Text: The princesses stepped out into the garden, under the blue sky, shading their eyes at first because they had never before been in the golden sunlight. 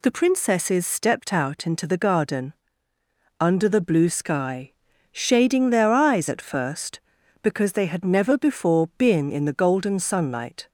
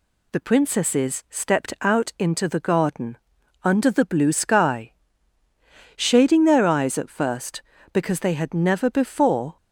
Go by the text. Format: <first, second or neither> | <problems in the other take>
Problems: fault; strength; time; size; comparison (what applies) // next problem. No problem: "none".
first | stops before "been in the golden sunlight"; at 9.5 s